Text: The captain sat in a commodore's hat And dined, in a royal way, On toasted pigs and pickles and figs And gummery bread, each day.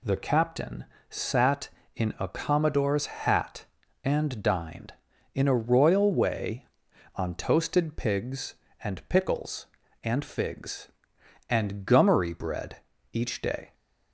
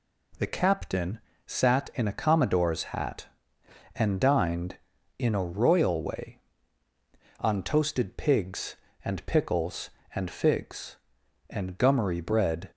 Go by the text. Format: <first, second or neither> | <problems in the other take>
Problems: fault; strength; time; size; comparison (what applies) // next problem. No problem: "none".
first | pauses between "captain" and "sat"; slight; at 1.1 s; 0.26 s long; slight in the first // stops before "each day"; at 12.7 s